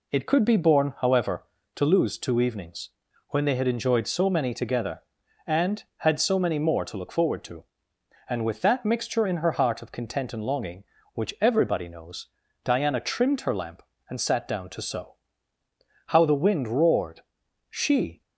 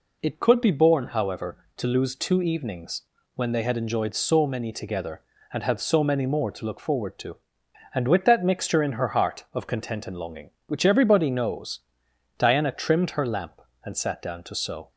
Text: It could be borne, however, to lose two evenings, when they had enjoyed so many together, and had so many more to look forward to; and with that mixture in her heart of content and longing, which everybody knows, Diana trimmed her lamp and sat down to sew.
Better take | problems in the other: second | goes on to say "How the wind roared She"; strong; from 16.0 s on; 2.1 s long

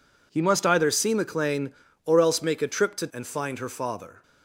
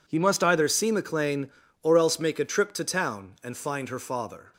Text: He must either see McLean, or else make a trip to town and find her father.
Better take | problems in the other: second | skips "town"; at 3.0 s

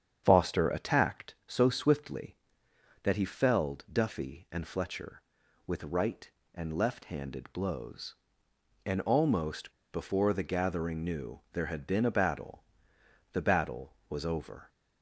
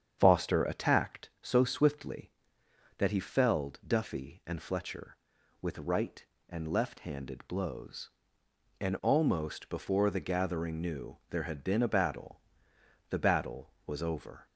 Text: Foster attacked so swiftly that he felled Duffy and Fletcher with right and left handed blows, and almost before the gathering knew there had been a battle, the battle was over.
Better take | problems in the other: second | starts louder than the rest; strong; until 1.2 s; 8 dB; strong in the second // pauses between "almost" and "before"; slight; at 9.7 s; 0.21 s long

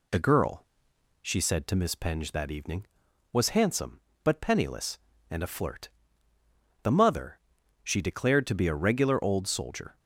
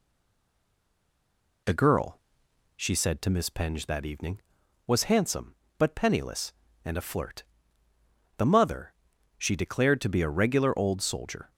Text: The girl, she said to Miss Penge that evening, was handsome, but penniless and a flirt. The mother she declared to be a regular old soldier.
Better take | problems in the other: first | stays silent before the first word; noticeable; until 1.6 s; 1.6 s long // pauses between "mother" and "she"; at 8.9 s; 0.44 s long; also in the first

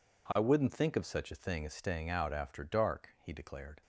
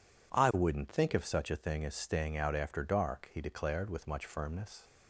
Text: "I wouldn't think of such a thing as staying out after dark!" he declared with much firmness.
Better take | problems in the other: second | stops before "with much firmness"; at 3.8 s

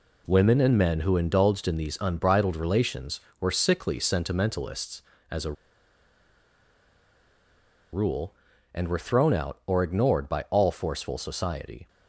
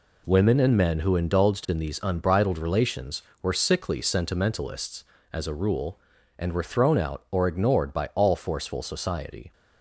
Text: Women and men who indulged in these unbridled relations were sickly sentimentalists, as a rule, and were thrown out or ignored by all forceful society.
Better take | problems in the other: second | pauses between "a" and "rule"; strong; at 5.5 s; 2.4 s long

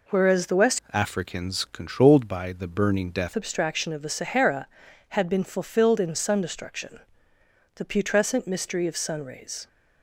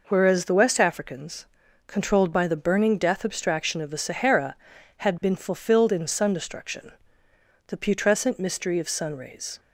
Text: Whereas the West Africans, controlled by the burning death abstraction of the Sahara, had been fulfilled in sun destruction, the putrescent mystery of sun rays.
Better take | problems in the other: second | changes voice from "Africans" to "death"; from 0.9 to 3.3 s; 2.4 s long

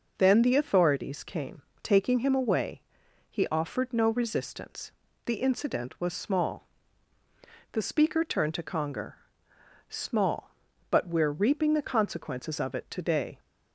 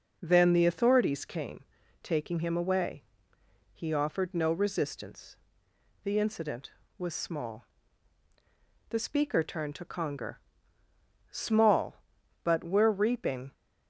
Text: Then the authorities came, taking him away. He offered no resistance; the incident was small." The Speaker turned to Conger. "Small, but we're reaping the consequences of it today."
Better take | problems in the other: first | stops before "the consequences of it today"; at 13.5 s

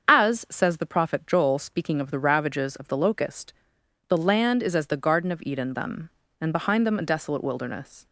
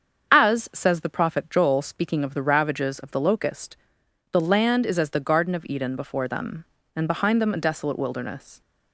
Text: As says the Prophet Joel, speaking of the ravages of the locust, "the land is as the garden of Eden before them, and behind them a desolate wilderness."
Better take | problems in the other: second | starts louder than the rest; until 1.1 s; 7 dB; strong in the second // skips "before"; at 5.7 s

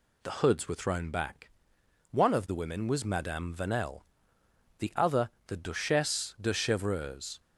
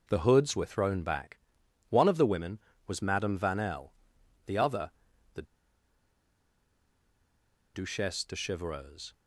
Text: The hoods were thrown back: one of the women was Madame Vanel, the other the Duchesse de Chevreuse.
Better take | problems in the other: first | pauses between "other" and "the"; at 4.9 s; 0.44 s long; slight in the first // pauses between "the" and "Duchesse"; strong; at 5.4 s; 2.3 s long

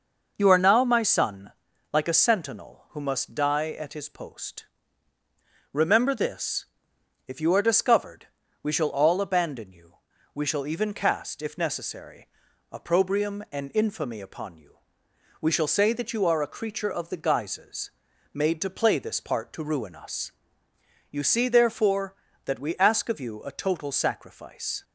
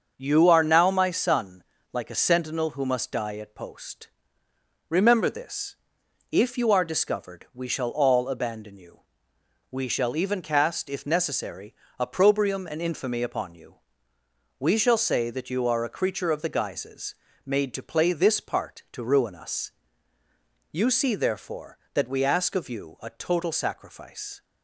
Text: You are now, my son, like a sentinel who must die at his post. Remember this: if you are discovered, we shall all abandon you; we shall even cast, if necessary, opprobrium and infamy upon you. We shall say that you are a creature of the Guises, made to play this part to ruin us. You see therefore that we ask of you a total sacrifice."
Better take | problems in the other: first | starts louder than the rest; until 1.1 s; 6.5 dB // skips "his"; at 3.5 s

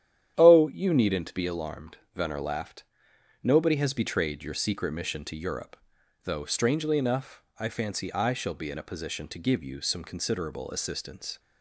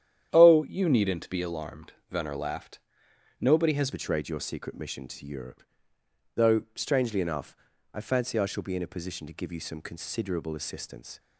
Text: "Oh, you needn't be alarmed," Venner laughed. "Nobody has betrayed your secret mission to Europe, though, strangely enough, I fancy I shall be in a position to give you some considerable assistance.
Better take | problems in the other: first | starts louder than the rest; strong; until 1.3 s; 10 dB; strong in the first // changes voice at "betrayed"; from 3.9 s on; 7.2 s long

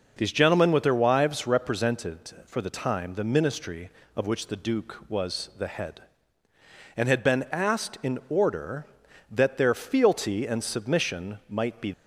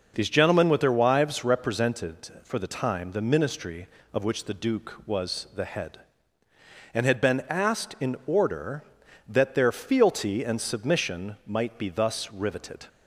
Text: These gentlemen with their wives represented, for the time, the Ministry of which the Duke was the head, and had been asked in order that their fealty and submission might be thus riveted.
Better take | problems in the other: second | stops before "thus riveted"; at 11.9 s

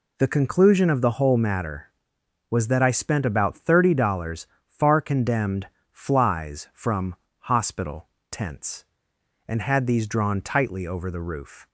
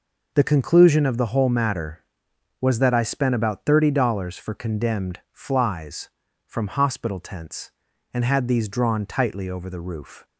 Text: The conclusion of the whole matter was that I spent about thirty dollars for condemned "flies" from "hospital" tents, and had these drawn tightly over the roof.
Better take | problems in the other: second | says "far" for "for"; at 4.6 s // pauses between "condemned" and "flies"; slight; at 5.6 s; 0.24 s long // pauses between "from" and "hospital"; slight; at 7.1 s; 0.24 s long // pauses between "hospital" and "tents"; slight; at 8.0 s; 0.24 s long

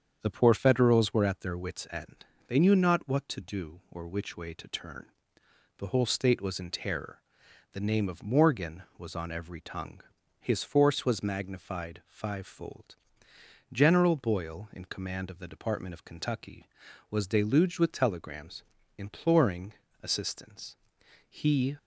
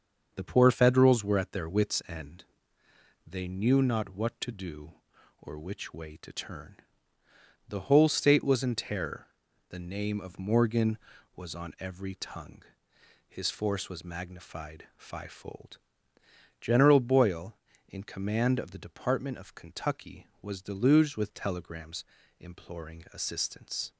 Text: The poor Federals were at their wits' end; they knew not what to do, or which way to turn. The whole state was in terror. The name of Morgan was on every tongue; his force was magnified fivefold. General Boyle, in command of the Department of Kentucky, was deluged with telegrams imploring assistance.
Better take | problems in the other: second | starts louder than the rest; strong; until 1.2 s; 7.5 dB; also in the second // pauses between "telegrams" and "imploring"; slight; at 18.6 s; 0.34 s long; slight in the second // pauses between "imploring" and "assistance"; slight; at 19.7 s; 0.28 s long // goes on to say "He"; slight; from 21.2 s on; 0.48 s long

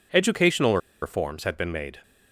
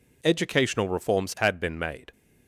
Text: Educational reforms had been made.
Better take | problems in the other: second | pauses between "Educational" and "reforms"; slight; at 0.7 s; 0.23 s long

